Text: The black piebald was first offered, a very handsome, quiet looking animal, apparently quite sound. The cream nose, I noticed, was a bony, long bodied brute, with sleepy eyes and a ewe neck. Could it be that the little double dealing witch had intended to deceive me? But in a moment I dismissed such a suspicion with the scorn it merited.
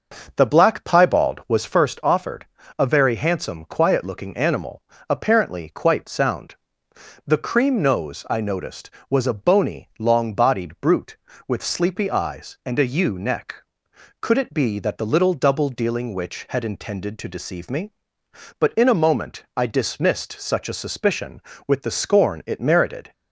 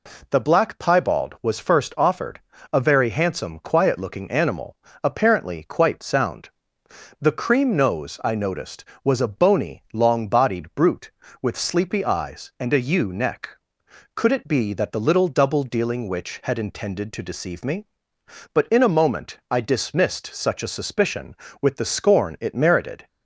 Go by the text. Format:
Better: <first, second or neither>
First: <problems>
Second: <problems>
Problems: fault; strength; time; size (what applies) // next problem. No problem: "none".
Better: second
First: starts louder than the rest; noticeable; until 1.8 s; 6 dB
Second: none